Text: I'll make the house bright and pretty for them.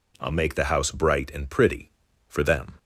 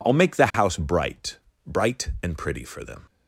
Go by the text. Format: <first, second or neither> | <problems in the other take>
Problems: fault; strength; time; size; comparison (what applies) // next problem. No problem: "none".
first | says "bright" twice; at 1.6 s